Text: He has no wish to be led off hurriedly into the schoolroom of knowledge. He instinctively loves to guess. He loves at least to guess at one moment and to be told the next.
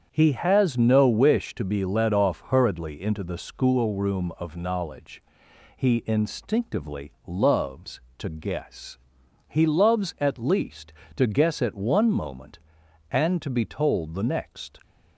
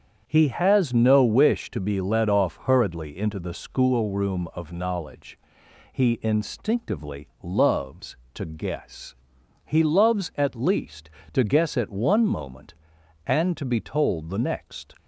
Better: neither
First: starts louder than the rest; strong; until 1.1 s; 7.5 dB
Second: starts louder than the rest; strong; until 1.2 s; 7.5 dB

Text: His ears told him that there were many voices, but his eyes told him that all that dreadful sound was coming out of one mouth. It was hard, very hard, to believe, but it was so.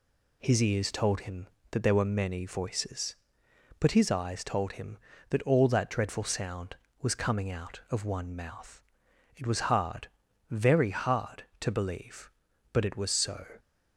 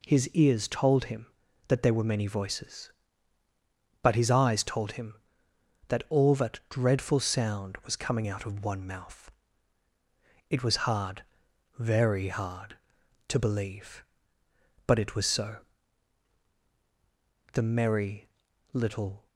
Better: first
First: none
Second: goes on to say "The Merry Little"; strong; from 17.5 s on; 1.7 s long

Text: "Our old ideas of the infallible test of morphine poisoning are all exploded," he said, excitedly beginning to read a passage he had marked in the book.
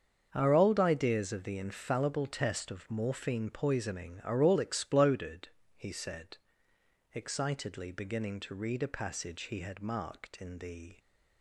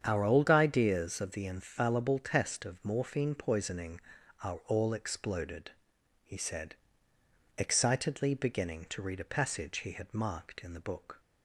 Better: second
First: starts louder than the rest; until 1.3 s; 6.5 dB // stops before "book"; at 10.9 s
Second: starts louder than the rest; strong; until 1.0 s; 8 dB

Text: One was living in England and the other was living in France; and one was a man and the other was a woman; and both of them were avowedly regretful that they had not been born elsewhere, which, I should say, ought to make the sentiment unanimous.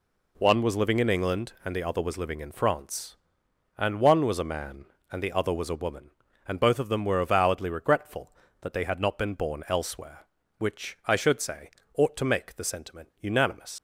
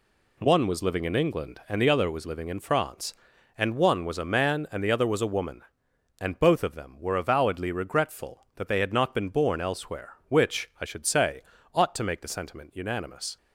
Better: second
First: leaves "unanimous" unfinished; at 13.7 s; 75 ms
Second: none

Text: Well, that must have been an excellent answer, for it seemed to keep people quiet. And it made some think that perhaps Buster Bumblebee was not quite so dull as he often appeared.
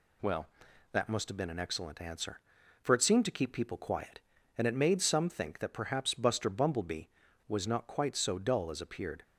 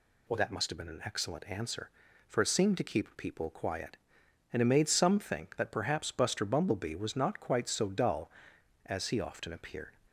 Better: second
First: skips "he often"; at 8.8 s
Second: none

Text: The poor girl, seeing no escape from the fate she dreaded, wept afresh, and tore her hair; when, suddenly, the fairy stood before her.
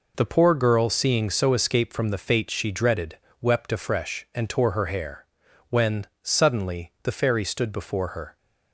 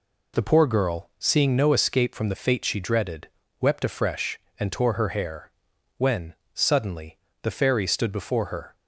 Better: second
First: says "so" for "no"; at 1.2 s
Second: none

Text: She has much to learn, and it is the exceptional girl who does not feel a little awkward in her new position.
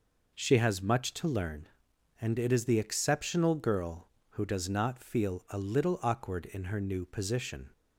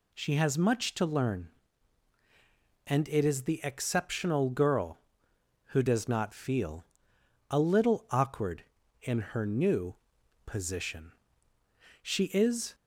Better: first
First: none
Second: pauses between "feel" and "a"; noticeable; at 6.8 s; 0.64 s long // pauses between "new" and "position"; noticeable; at 9.9 s; 0.50 s long // goes on to say "She is"; noticeable; from 12.0 s on; 0.72 s long

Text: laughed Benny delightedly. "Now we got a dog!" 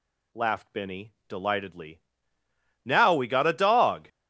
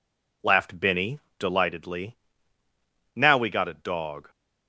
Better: neither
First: pauses between "Benny" and "delightedly"; slight; at 1.1 s; 0.16 s long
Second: pauses between "Benny" and "delightedly"; slight; at 1.1 s; 0.18 s long

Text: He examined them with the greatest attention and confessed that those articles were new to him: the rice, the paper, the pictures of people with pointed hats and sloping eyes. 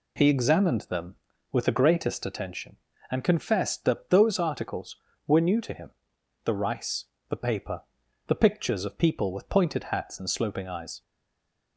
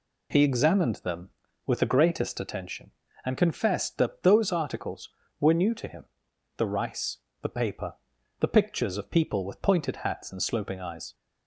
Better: second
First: stays silent after the last word; slight; from 11.0 s on; 0.7 s long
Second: none

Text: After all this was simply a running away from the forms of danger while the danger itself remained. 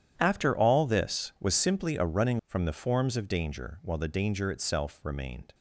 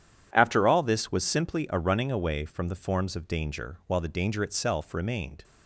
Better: second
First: starts louder than the rest; strong; until 1.1 s; 10 dB // skips "away"; at 2.4 s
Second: none

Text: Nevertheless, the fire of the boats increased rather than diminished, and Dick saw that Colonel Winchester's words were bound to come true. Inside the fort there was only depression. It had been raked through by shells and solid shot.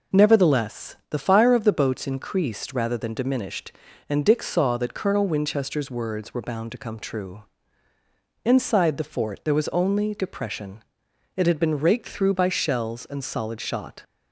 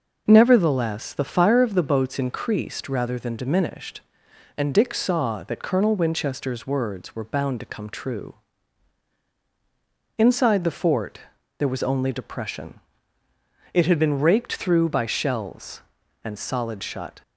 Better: first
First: none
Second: pauses between "fort" and "there"; at 11.1 s; 0.38 s long // says "shut" for "shot"; at 16.8 s

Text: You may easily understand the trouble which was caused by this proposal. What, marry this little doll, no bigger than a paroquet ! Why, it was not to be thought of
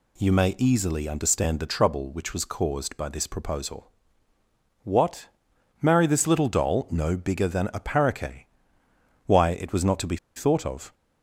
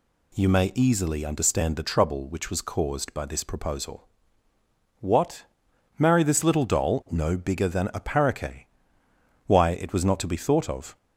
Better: second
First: pauses between "be" and "thought"; slight; at 10.1 s; 0.19 s long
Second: none

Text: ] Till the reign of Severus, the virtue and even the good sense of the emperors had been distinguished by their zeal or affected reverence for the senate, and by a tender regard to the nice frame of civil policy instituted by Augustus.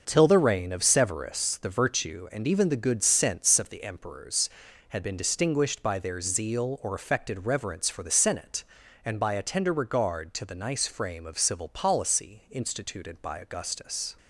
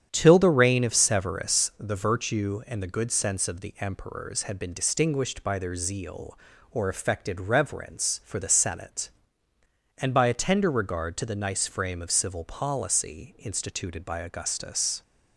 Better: first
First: starts louder than the rest; until 1.0 s; 6.5 dB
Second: starts louder than the rest; strong; until 1.1 s; 9 dB // skips "even"; at 2.8 s

